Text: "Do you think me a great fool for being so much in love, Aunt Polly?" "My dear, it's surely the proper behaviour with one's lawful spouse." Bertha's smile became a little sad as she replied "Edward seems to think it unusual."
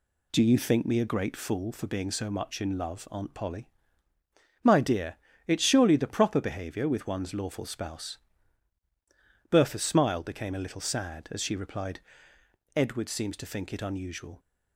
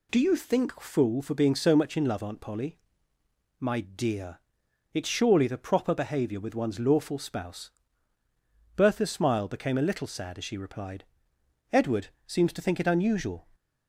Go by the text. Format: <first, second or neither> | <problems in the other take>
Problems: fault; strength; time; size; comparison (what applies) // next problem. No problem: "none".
first | skips "me a great"; at 0.8 s // pauses between "replied" and "Edward"; noticeable; at 11.0 s; 0.66 s long; noticeable in the first // pauses between "Edward" and "seems"; slight; at 12.0 s; 0.18 s long